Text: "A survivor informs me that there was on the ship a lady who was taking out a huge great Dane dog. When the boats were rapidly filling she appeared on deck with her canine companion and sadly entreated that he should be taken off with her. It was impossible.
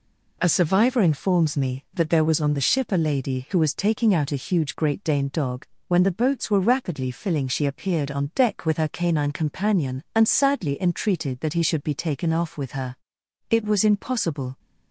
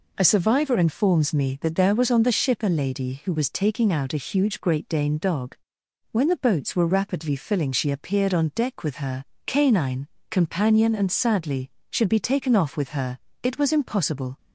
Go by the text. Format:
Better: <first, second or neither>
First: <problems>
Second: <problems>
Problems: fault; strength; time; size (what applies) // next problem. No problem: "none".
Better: first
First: none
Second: pauses between "her" and "canine"; slight; at 9.2 s; 0.21 s long // pauses between "canine" and "companion"; slight; at 10.0 s; 0.22 s long // skips "entreated that he"; at 11.7 s